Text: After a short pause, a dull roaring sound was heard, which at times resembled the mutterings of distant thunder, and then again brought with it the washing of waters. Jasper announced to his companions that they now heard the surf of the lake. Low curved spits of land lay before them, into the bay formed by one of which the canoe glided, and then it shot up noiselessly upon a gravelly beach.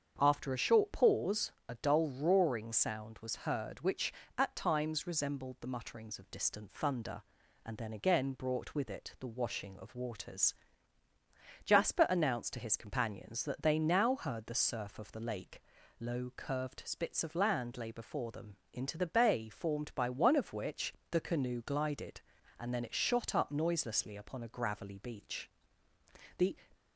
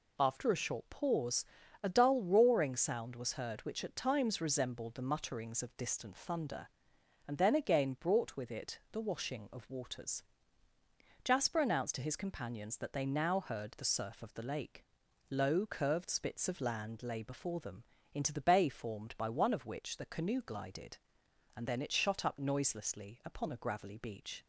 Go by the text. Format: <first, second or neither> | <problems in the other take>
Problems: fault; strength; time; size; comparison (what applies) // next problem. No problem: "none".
second | starts louder than the rest; strong; until 1.1 s; 7.5 dB // pauses between "which" and "the"; slight; at 20.9 s; 0.18 s long // goes on to say "The"; slight; from 26.3 s on; 0.16 s long